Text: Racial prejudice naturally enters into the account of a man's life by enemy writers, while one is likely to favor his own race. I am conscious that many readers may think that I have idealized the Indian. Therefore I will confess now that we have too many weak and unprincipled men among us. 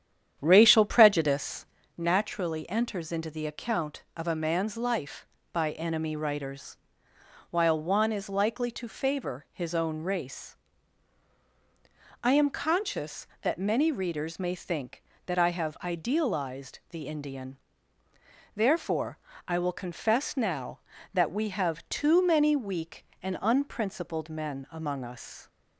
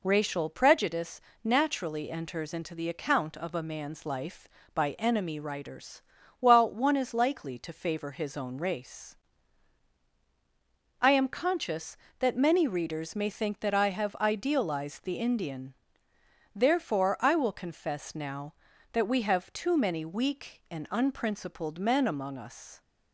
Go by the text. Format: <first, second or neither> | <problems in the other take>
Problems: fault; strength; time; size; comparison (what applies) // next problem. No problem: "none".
second | starts louder than the rest; strong; until 1.9 s; 9.5 dB // pauses between "prejudice" and "naturally"; slight; at 1.6 s; 0.30 s long; slight in the second // pauses between "Therefore" and "I"; slight; at 19.1 s; 0.32 s long